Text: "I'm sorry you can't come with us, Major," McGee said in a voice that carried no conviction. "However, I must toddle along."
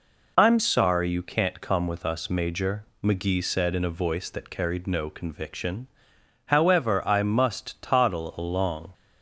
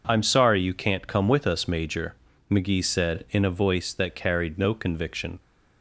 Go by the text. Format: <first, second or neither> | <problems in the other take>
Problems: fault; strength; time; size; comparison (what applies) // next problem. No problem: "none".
first | stops before "However I must toddle along"; at 5.3 s